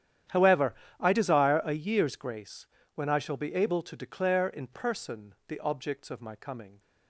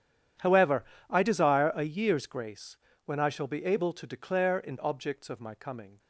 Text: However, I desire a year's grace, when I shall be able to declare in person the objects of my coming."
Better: first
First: starts louder than the rest; strong; until 1.5 s; 10.5 dB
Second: starts louder than the rest; strong; until 1.6 s; 9.5 dB // skips "person the"; at 4.7 s

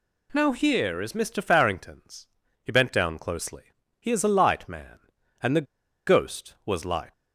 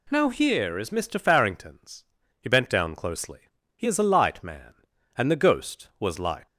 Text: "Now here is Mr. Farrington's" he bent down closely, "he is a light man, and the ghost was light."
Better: second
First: pauses between "Farrington's" and "he"; slight; at 2.2 s; 0.34 s long // pauses between "the" and "ghost"; at 5.6 s; 0.41 s long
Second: pauses between "Farrington's" and "he"; slight; at 2.0 s; 0.34 s long

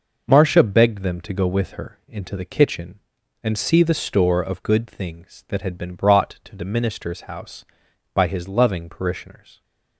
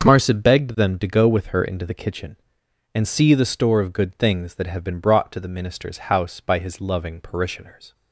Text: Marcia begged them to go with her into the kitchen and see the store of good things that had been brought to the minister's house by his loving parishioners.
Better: first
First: none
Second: starts louder than the rest; until 1.0 s; 6.5 dB // says "have" for "had"; at 4.6 s

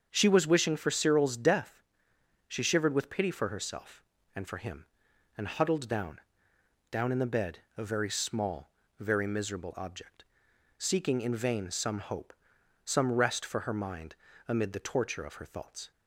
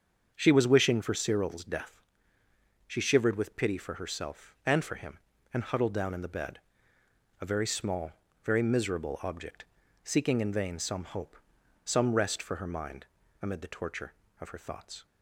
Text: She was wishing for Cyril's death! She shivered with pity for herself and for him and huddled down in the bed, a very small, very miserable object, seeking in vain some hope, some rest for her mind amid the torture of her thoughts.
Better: second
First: starts louder than the rest; until 1.1 s; 7 dB // says "down" twice; at 6.9 s // pauses between "mind" and "amid"; slight; at 14.1 s; 0.32 s long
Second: starts louder than the rest; until 1.3 s; 7 dB // pauses between "mind" and "amid"; slight; at 13.0 s; 0.36 s long

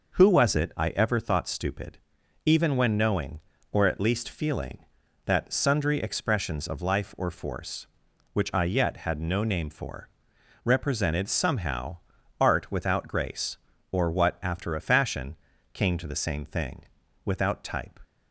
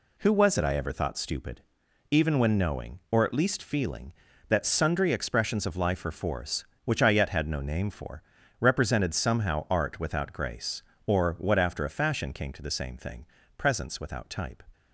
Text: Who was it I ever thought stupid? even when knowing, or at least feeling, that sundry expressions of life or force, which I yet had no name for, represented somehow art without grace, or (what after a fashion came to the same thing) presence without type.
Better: second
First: pauses between "somehow" and "art"; noticeable; at 11.9 s; 0.46 s long // pauses between "fashion" and "came"; slight; at 15.3 s; 0.34 s long // skips "presence"; at 17.0 s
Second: none

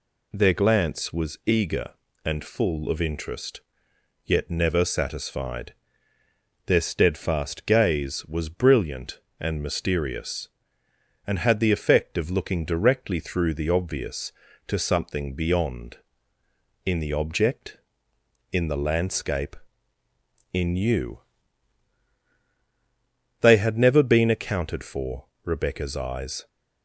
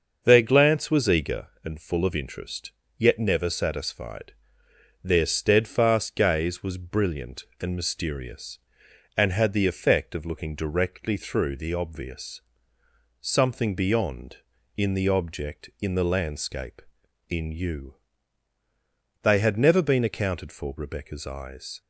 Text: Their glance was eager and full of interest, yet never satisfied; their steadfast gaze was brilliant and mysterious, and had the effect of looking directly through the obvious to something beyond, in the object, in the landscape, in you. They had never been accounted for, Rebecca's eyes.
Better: first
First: none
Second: starts louder than the rest; until 1.2 s; 6.5 dB // skips "to"; at 12.8 s

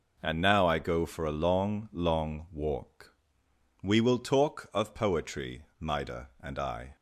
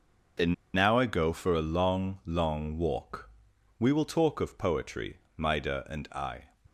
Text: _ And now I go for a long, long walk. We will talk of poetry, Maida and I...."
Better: first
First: none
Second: pauses between "And" and "now"; slight; at 0.5 s; 0.19 s long

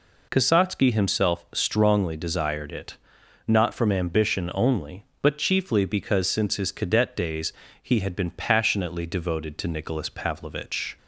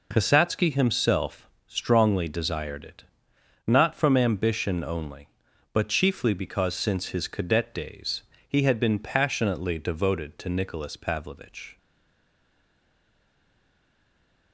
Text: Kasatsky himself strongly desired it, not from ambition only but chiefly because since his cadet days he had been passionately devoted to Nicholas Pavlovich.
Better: first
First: pauses between "days" and "he"; slight; at 7.5 s; 0.28 s long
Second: pauses between "himself" and "strongly"; slight; at 1.4 s; 0.20 s long // pauses between "days" and "he"; slight; at 8.2 s; 0.24 s long // stays silent after the last word; strong; from 11.7 s on; 2.8 s long

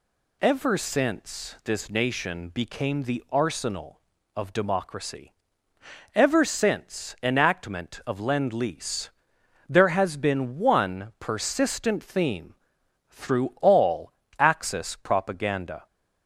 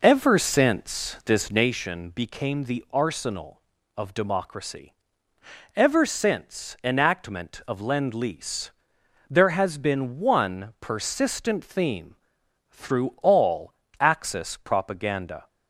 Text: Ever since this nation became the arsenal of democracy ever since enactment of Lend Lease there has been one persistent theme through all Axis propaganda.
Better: first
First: pauses between "democracy" and "ever"; noticeable; at 5.3 s; 0.82 s long // pauses between "Lease" and "there"; noticeable; at 9.0 s; 0.58 s long // pauses between "theme" and "through"; noticeable; at 12.5 s; 0.54 s long // pauses between "all" and "Axis"; slight; at 14.1 s; 0.26 s long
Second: starts louder than the rest; noticeable; until 1.8 s; 4.5 dB // pauses between "democracy" and "ever"; noticeable; at 4.9 s; 0.82 s long // pauses between "Lease" and "there"; noticeable; at 8.6 s; 0.58 s long // pauses between "theme" and "through"; noticeable; at 12.1 s; 0.54 s long // pauses between "all" and "Axis"; slight; at 13.7 s; 0.26 s long

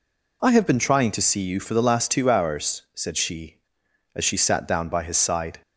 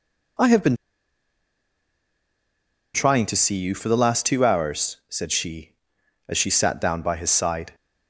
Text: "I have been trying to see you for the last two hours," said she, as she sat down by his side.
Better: first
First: none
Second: pauses between "been" and "trying"; strong; at 0.7 s; 2.1 s long

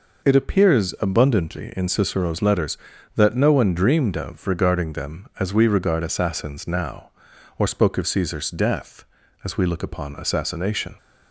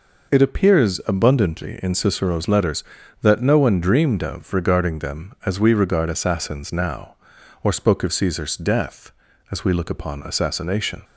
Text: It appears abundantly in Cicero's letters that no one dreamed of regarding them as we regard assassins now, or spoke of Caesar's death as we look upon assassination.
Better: neither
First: none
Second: none

